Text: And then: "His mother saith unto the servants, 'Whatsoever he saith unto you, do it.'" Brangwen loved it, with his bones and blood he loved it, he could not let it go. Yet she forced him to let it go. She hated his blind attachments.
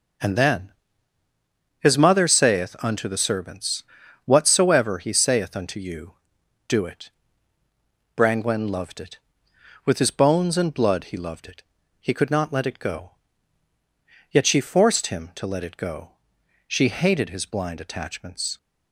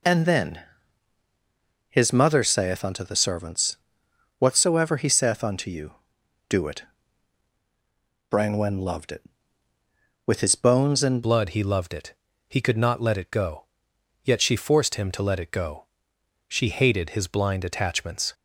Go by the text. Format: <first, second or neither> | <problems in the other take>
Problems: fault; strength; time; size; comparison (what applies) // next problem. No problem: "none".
first | changes voice at "blood"; from 11.2 s on; 7.1 s long